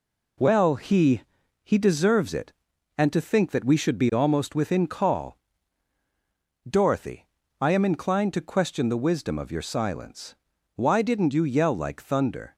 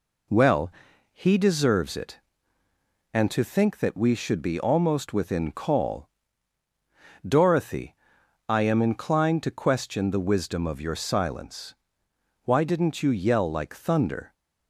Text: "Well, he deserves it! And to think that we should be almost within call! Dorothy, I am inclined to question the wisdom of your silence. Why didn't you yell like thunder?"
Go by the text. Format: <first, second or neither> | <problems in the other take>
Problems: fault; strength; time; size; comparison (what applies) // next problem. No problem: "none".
second | says "he" twice; at 1.6 s